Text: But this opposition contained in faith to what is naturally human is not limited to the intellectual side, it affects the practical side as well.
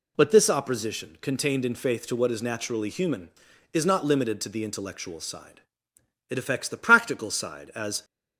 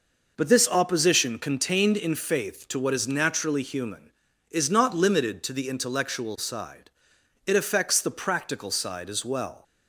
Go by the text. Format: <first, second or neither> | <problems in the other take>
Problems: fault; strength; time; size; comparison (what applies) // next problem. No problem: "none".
second | stops before "well"; at 8.0 s